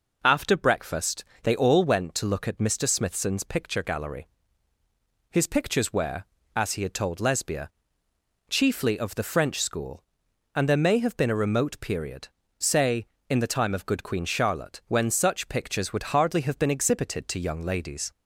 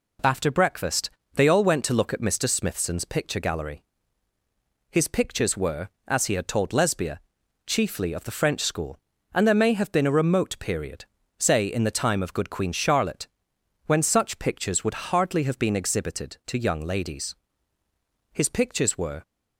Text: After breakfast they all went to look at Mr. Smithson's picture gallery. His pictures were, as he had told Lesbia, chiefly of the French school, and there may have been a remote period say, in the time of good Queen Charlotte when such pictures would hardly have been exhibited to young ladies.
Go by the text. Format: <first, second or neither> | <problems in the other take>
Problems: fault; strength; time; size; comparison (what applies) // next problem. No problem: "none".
first | pauses between "breakfast" and "they"; slight; at 1.1 s; 0.24 s long; slight in the first // pauses between "period" and "say"; slight; at 11.0 s; 0.34 s long; slight in the first // pauses between "Charlotte" and "when"; noticeable; at 13.2 s; 0.60 s long // goes on to say "His pictures were"; noticeable; from 18.3 s on; 0.90 s long